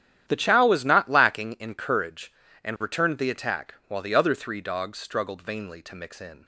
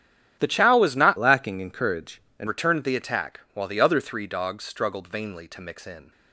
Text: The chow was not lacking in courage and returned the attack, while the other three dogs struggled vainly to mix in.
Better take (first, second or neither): first